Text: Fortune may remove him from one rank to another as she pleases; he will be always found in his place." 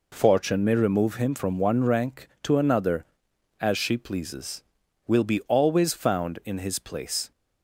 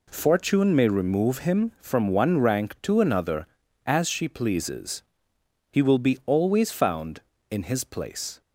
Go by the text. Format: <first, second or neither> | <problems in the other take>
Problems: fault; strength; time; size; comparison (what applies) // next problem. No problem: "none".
second | skips "he"; at 4.8 s